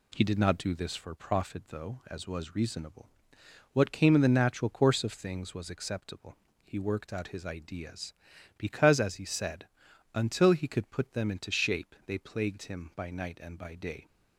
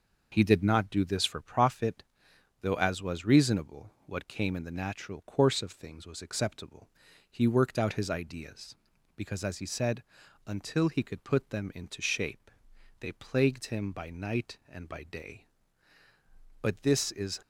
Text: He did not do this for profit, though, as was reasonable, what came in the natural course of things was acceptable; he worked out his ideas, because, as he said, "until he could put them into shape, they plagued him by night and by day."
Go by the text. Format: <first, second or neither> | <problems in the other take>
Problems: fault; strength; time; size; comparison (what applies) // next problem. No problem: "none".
first | goes on to say "But this is"; noticeable; from 16.6 s on; 0.76 s long